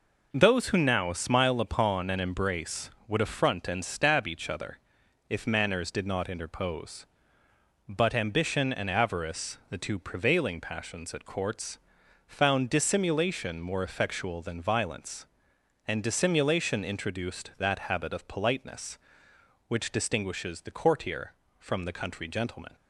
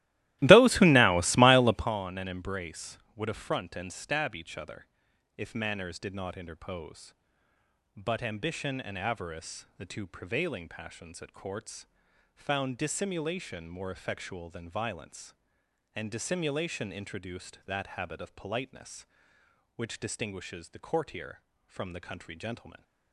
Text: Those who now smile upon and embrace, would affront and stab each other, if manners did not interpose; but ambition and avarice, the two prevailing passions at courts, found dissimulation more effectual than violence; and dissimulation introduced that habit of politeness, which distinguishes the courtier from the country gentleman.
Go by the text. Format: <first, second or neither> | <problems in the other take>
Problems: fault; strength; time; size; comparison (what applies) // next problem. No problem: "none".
first | starts louder than the rest; strong; until 1.9 s; 16 dB